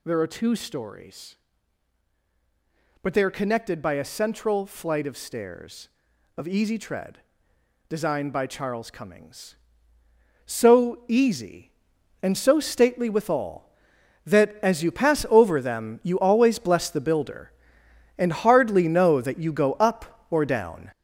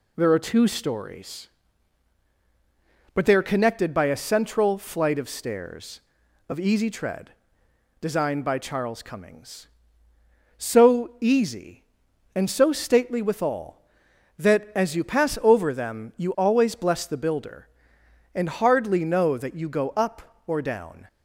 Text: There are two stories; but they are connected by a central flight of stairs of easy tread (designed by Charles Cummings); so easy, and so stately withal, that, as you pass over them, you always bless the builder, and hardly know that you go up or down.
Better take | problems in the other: second | gets louder; throughout; 6.5 dB

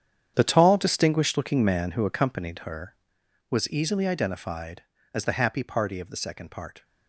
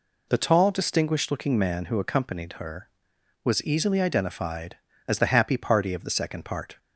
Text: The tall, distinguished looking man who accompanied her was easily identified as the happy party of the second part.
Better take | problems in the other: second | gets quieter; strong; throughout; 14 dB

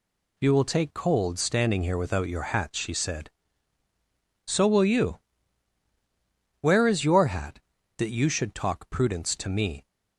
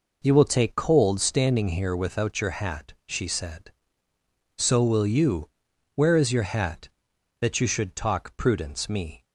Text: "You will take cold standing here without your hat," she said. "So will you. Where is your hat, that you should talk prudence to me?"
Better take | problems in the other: first | skips "to"; at 8.8 s

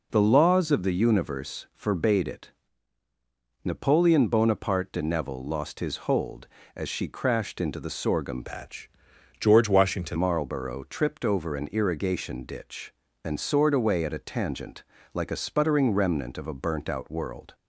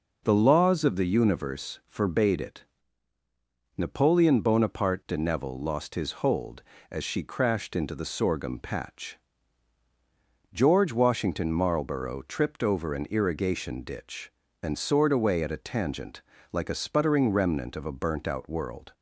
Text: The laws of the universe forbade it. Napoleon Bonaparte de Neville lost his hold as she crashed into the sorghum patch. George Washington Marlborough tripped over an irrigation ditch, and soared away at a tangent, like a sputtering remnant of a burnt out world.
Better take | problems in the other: second | changes voice from "patch" to "Washington"; from 8.4 to 10.1 s; 1.7 s long

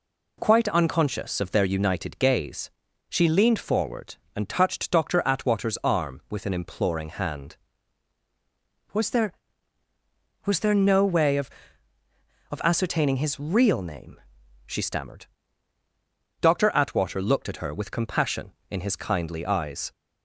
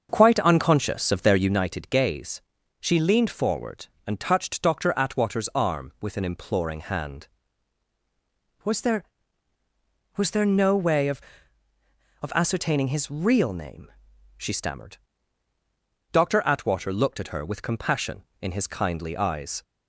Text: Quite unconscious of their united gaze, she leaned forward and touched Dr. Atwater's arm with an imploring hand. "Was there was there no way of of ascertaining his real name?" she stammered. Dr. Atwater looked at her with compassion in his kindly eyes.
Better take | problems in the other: first | starts louder than the rest; until 1.6 s; 6.5 dB

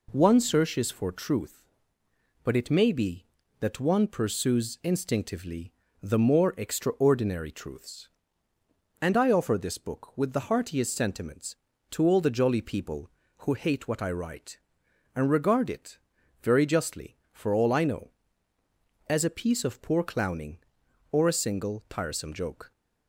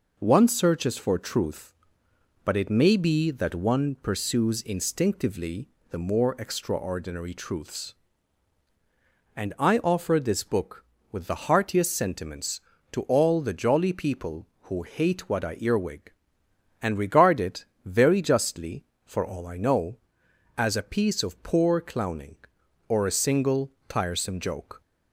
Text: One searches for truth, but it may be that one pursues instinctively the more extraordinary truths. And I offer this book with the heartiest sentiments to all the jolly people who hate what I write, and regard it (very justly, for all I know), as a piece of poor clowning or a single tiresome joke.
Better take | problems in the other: first | pauses between "instinctively" and "the"; slight; at 5.6 s; 0.22 s long; slight in the first // says "earwig" for "write"; at 15.5 s // pauses between "single" and "tiresome"; slight; at 23.6 s; 0.18 s long

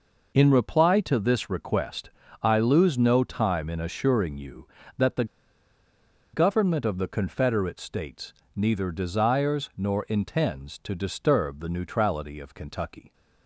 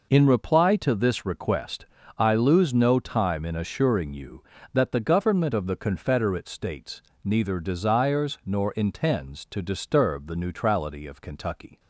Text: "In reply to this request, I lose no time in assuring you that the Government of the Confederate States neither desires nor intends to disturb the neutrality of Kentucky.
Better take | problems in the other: second | pauses between "the" and "Government"; at 5.2 s; 1.0 s long // pauses between "States" and "neither"; slight; at 8.3 s; 0.22 s long; slight in the second

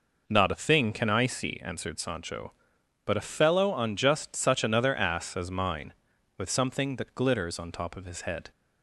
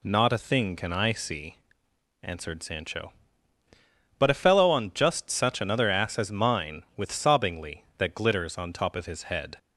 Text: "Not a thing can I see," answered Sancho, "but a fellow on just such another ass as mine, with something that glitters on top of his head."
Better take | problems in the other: first | says "sobbingly" for "something"; at 7.1 s

